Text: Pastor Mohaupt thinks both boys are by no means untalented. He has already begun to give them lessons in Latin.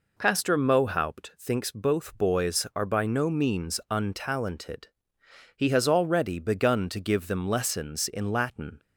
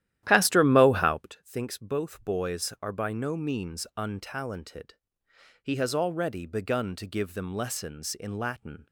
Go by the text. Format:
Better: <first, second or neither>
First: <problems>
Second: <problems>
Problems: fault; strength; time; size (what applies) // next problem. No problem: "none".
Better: first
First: none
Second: starts louder than the rest; strong; until 1.4 s; 12.5 dB